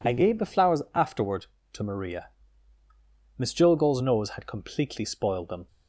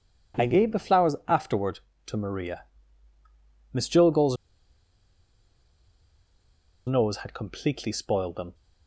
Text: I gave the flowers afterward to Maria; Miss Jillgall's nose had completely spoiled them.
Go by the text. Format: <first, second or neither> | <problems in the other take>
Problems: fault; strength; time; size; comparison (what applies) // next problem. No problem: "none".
first | pauses between "Jillgall's" and "nose"; strong; at 4.3 s; 2.5 s long